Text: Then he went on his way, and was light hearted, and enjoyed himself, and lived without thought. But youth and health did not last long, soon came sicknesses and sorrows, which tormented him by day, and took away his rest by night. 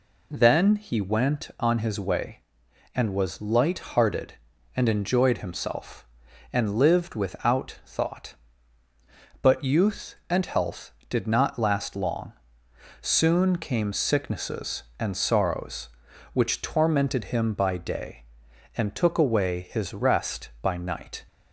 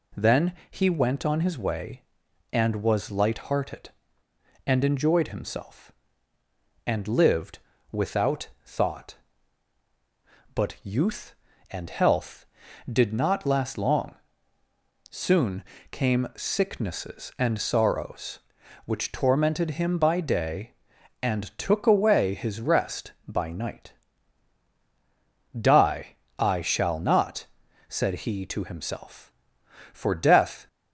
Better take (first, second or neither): first